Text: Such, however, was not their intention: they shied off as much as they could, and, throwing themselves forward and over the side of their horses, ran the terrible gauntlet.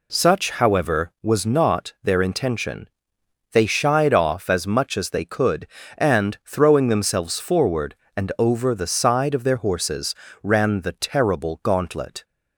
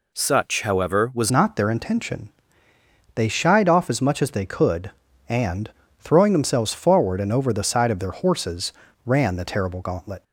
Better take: first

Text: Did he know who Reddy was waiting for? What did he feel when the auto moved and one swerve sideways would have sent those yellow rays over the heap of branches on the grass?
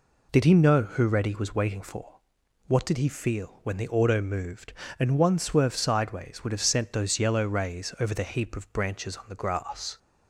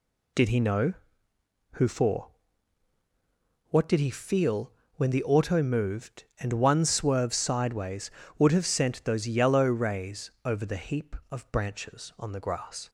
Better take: first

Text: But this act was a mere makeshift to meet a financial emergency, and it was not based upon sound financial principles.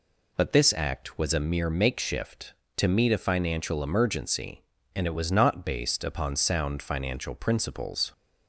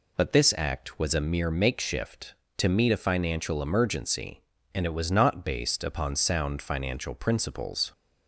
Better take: neither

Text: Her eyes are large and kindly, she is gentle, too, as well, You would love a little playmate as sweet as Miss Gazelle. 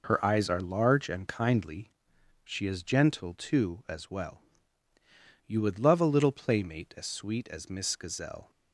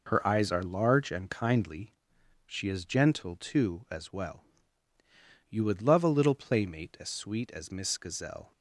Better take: neither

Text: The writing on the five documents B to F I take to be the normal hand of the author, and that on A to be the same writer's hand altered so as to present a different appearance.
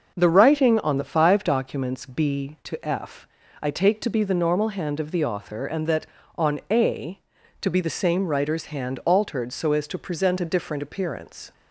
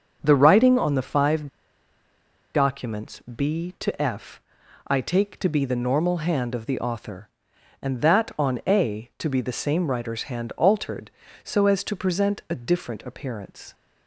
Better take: first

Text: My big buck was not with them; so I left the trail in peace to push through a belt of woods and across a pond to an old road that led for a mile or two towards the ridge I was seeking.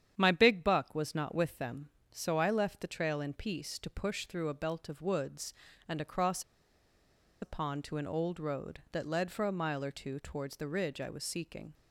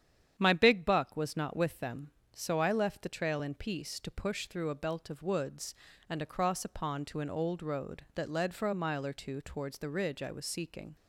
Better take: second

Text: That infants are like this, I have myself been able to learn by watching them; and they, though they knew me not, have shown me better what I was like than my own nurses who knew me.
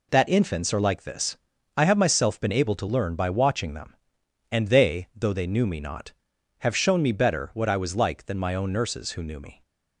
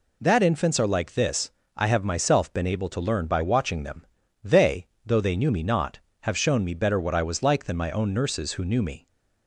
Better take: first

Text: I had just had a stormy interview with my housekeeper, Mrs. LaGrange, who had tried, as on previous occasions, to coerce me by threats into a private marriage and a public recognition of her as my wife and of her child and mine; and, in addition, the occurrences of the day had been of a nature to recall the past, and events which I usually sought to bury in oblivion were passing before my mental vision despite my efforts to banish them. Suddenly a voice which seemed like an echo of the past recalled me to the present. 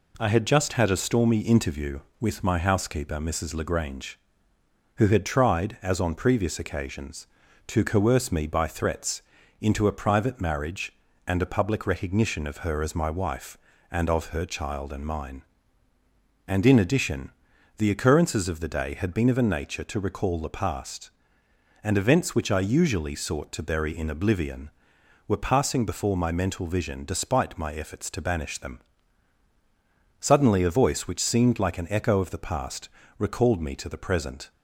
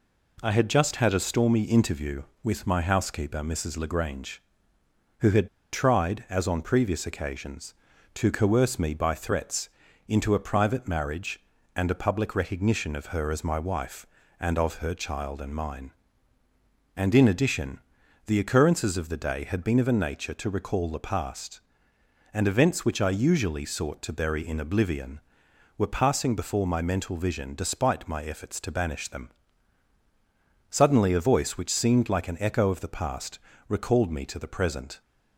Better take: first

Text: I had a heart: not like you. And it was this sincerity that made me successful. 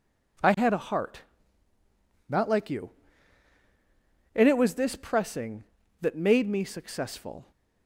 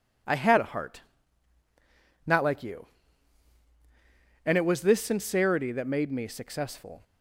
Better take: second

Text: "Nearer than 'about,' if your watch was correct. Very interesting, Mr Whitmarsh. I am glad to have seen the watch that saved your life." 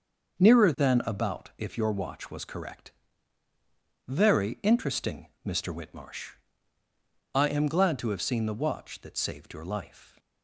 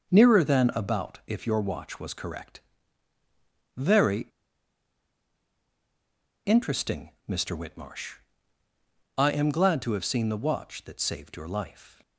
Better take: first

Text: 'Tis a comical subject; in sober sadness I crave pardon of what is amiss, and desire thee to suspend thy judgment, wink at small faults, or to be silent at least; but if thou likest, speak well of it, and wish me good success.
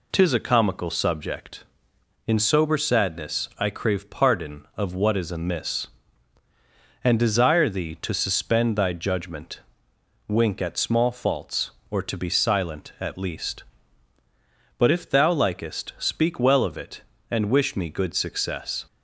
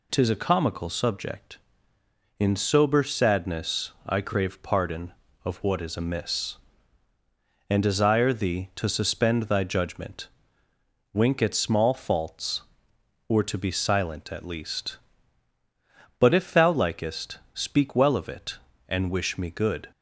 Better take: first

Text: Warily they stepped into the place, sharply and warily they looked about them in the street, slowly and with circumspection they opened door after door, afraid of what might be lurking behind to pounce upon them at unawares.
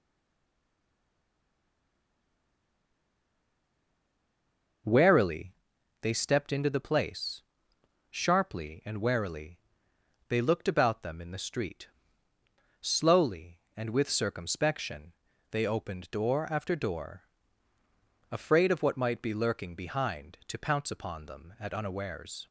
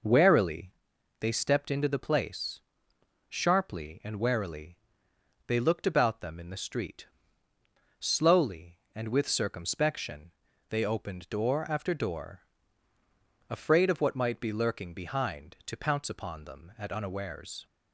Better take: second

